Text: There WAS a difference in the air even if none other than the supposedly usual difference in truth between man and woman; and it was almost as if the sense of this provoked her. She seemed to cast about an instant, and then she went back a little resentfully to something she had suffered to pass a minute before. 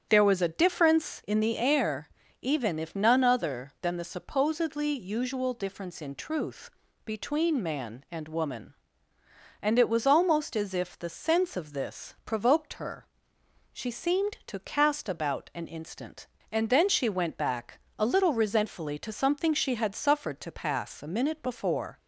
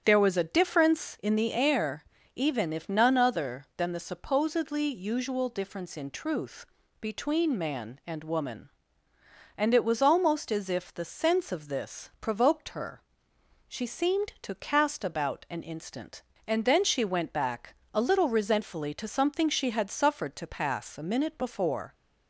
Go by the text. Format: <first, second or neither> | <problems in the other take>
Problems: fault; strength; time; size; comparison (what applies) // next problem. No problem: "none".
neither | starts louder than the rest; strong; the same in both // pauses between "air" and "even"; slight; the same in both // pauses between "truth" and "between"; the same in both // pauses between "back" and "a"; slight; the same in both